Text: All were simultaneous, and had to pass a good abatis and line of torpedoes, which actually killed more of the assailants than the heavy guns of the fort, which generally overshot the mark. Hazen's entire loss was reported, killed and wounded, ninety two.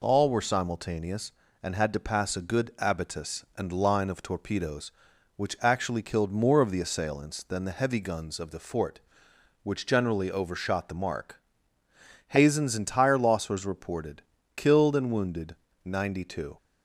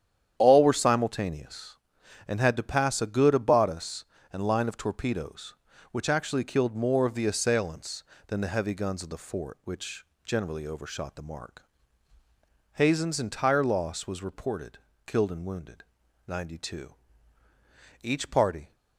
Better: first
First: none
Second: starts louder than the rest; strong; until 1.3 s; 9.5 dB // pauses between "which" and "generally"; slight; at 10.0 s; 0.20 s long // goes on to say "Each party"; noticeable; from 18.0 s on; 0.72 s long

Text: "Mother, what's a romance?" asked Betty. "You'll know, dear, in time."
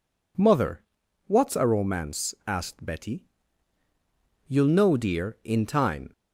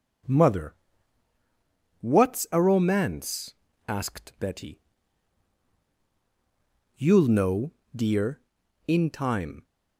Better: neither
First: none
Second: none

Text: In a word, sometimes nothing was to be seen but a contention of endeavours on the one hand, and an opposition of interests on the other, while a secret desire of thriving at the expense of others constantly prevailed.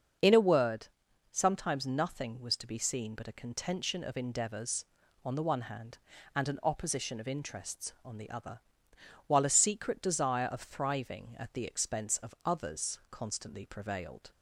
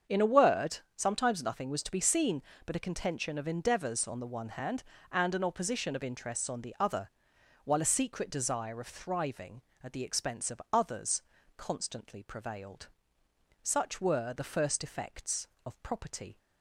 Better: first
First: starts louder than the rest; until 1.6 s; 6.5 dB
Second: starts louder than the rest; until 1.2 s; 7 dB // pauses between "others" and "constantly"; slight; at 11.2 s; 0.34 s long // goes on to say "Such were the first effects of property"; strong; from 13.6 s on; 2.7 s long

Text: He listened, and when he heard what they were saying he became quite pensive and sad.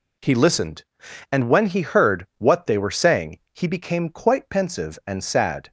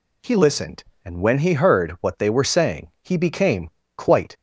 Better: first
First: none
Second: pauses between "became" and "quite"; slight; at 3.7 s; 0.26 s long // stops before "pensive and sad"; at 4.3 s

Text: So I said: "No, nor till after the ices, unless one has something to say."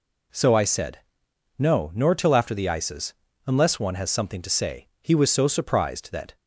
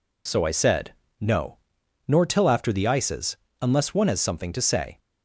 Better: second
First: goes on to say "He was so surprised that"; from 5.0 s on; 1.3 s long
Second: none

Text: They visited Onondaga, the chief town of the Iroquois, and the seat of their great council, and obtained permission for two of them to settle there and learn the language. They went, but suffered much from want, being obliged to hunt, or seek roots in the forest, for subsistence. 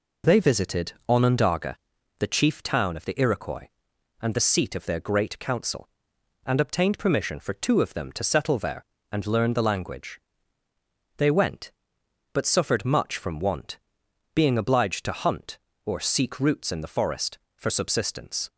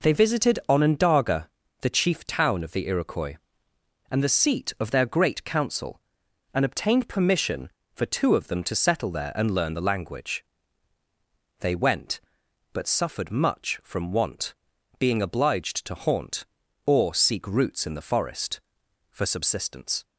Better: first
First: none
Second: says "haunt" for "hunt"; at 15.9 s

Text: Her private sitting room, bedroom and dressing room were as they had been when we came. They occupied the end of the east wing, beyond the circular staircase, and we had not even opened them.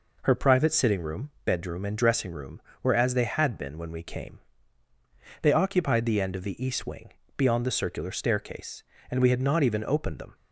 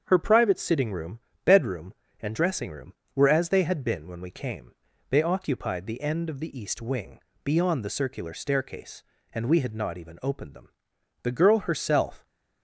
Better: first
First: none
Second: starts louder than the rest; strong; until 1.0 s; 7.5 dB // goes on to say "The girl herself"; noticeable; from 11.2 s on; 1.0 s long

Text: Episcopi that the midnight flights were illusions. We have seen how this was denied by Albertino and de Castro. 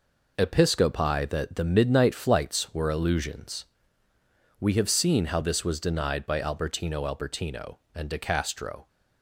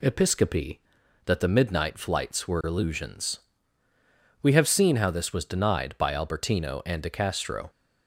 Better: second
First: says "Albertino" twice; at 7.0 s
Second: none

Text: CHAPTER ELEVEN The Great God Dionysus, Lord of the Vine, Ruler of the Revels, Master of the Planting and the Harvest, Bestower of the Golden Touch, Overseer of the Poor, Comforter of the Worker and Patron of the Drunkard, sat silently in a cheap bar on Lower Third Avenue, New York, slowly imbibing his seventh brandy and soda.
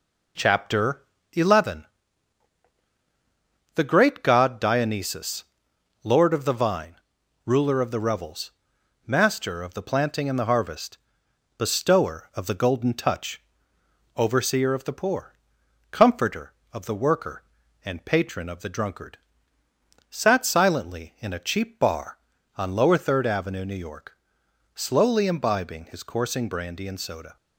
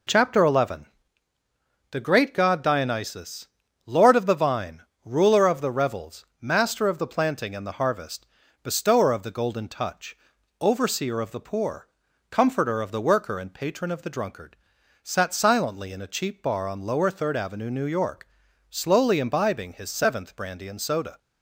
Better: second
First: pauses between "CHAPTER" and "ELEVEN"; slight; at 1.0 s; 0.30 s long // pauses between "ELEVEN" and "The"; strong; at 1.8 s; 1.8 s long // says "coursing" for "seventh"; at 26.0 s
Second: pauses between "ELEVEN" and "The"; at 0.8 s; 1.0 s long

